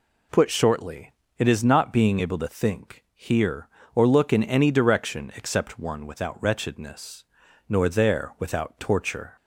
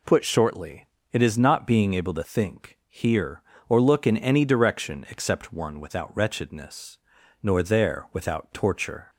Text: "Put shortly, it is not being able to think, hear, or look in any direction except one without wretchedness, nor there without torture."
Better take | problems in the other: neither | none

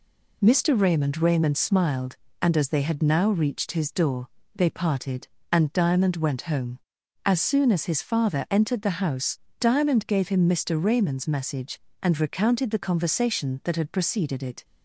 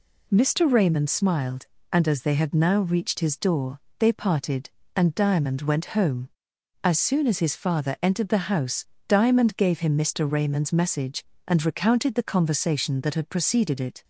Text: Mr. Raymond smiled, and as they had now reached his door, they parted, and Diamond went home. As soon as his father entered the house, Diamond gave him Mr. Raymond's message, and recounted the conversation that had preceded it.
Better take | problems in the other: second | says "Raymond" twice; at 1.1 s

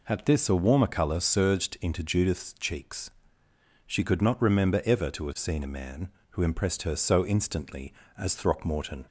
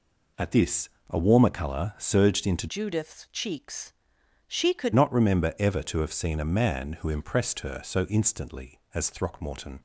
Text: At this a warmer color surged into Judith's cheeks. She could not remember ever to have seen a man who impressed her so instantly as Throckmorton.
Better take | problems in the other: first | pauses between "this" and "a"; slight; at 0.8 s; 0.22 s long // changes voice from "Judith's" to "could"; from 2.6 to 4.9 s; 2.3 s long

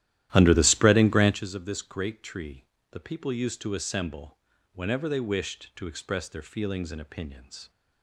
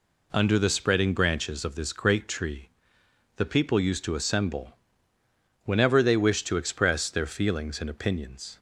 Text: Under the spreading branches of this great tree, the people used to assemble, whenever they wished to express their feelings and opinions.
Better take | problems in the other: second | starts louder than the rest; strong; until 1.4 s; 13 dB

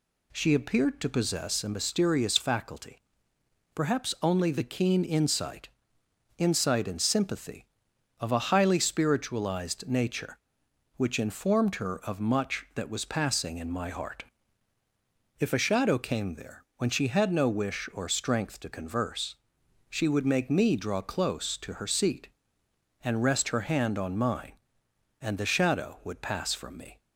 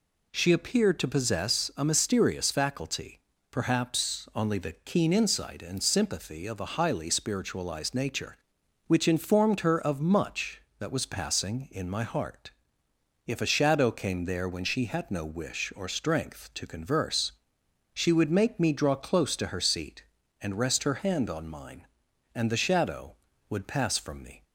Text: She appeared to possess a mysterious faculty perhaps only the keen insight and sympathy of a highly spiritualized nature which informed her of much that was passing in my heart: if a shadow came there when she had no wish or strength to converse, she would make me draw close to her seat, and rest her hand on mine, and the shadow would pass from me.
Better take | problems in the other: second | pauses between "faculty" and "perhaps"; noticeable; at 2.9 s; 0.76 s long; slight in the second // says "insight" twice; at 6.3 s

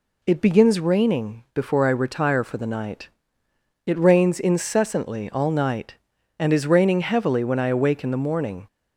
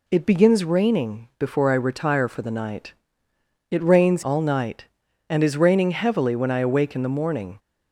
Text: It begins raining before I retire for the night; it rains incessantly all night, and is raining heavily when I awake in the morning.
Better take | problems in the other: first | skips "incessantly"; at 4.2 s

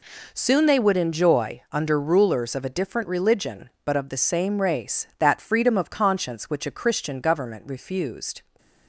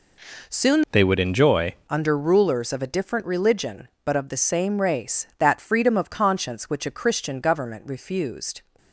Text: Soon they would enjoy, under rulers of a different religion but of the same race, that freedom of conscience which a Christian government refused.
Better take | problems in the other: first | changes voice from "they" to "enjoy"; from 0.9 to 1.7 s; 0.8 s long

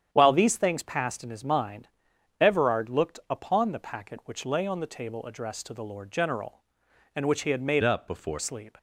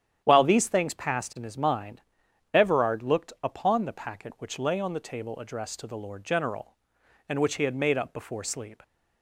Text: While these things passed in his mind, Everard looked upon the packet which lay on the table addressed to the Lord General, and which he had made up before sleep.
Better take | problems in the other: second | starts louder than the rest; strong; until 1.1 s; 8.5 dB; strong in the second // changes voice from "up" to "before"; from 7.8 to 8.4 s; 0.6 s long

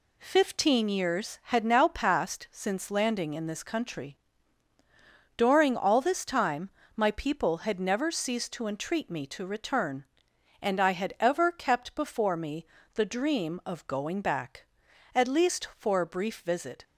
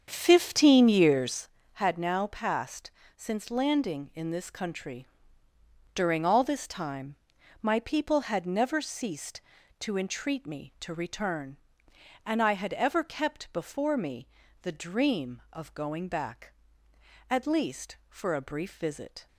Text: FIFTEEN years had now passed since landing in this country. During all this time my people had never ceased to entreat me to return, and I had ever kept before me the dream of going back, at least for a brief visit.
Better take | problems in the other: first | starts louder than the rest; strong; until 1.5 s; 7 dB // pauses between "passed" and "since"; slight; at 2.8 s; 0.26 s long // pauses between "time" and "my"; noticeable; at 7.1 s; 0.46 s long; slight in the first // pauses between "me" and "the"; slight; at 14.2 s; 0.36 s long; slight in the first

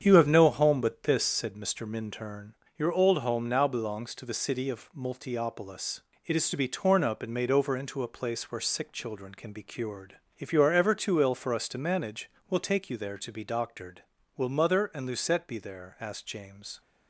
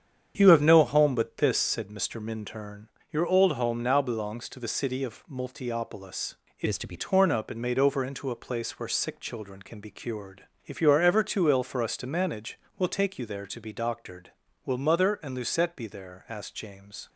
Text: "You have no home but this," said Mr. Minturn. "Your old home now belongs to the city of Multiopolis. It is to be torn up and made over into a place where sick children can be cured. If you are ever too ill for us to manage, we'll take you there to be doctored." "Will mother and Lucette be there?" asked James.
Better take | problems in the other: first | starts louder than the rest; strong; until 1.3 s; 8 dB; strong in the first // changes voice from "is" to "be"; from 6.6 to 6.9 s; 0.3 s long

